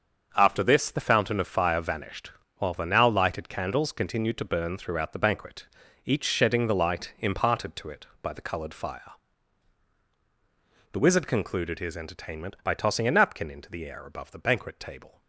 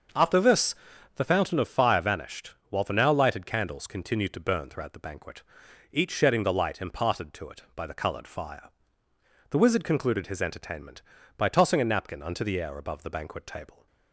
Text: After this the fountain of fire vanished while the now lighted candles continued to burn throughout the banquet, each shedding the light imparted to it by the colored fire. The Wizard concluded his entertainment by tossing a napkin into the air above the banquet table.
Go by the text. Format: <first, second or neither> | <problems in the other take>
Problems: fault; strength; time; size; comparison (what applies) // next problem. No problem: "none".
first | starts louder than the rest; until 1.5 s; 6.5 dB; also in the first // pauses between "this" and "the"; at 0.7 s; 0.42 s long // pauses between "vanished" and "while"; slight; at 2.5 s; 0.18 s long; slight in the first // says "unto" for "into"; at 12.2 s